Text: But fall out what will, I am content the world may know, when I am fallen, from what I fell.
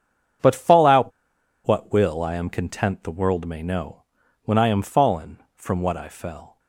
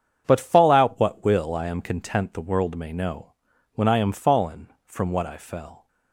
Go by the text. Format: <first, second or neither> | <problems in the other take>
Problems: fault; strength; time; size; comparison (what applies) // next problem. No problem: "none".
second | starts louder than the rest; strong; until 1.9 s; 8 dB; strong in the second // pauses between "out" and "what"; noticeable; at 1.1 s; 0.55 s long